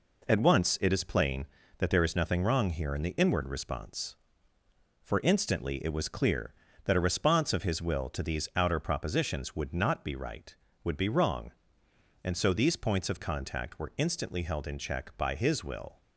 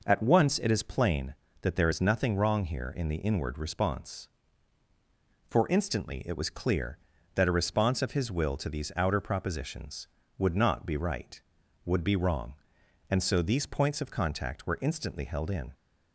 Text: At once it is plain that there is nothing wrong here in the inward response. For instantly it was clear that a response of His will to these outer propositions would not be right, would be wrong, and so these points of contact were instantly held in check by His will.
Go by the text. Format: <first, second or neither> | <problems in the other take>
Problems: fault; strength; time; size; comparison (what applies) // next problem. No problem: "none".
first | stops before "check by His will"; at 15.7 s